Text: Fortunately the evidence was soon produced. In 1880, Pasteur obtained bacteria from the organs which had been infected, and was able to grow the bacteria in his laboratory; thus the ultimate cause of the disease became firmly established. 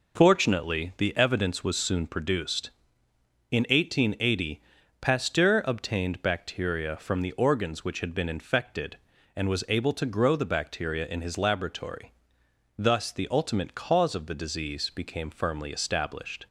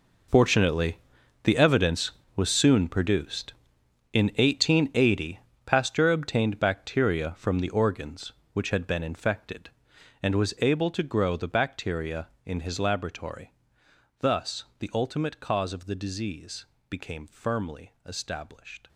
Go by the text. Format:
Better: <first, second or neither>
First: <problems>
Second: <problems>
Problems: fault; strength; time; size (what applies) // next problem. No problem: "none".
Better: first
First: none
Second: gets quieter; strong; throughout; 15 dB // pauses between "Fortunately" and "the"; noticeable; at 0.9 s; 0.46 s long // pauses between "disease" and "became"; slight; at 16.6 s; 0.24 s long